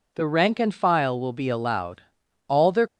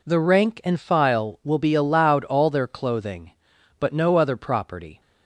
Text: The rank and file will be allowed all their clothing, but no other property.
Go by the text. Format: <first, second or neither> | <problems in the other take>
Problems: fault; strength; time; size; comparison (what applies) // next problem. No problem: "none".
second | pauses between "allowed" and "all"; at 2.0 s; 0.44 s long // stops before "clothing but no other property"; at 2.8 s